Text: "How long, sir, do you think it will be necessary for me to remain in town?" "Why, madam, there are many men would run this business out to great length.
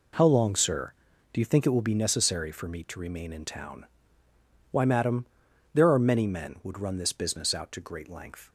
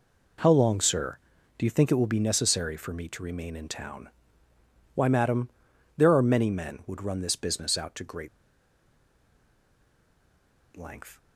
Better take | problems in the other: first | pauses between "great" and "length"; strong; at 8.2 s; 2.4 s long

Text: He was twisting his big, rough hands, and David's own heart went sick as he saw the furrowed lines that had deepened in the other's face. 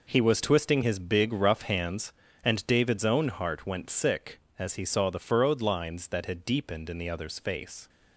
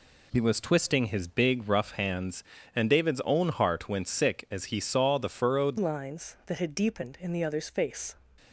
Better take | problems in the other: first | changes voice at "lines"; from 5.7 s on; 2.4 s long

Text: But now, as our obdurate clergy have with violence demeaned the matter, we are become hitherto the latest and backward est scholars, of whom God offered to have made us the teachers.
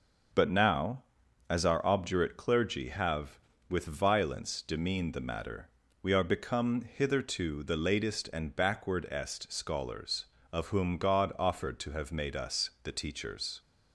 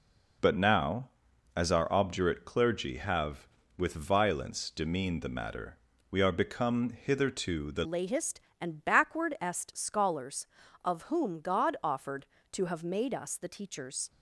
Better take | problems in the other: first | changes voice at "latest"; from 7.8 s on; 6.2 s long

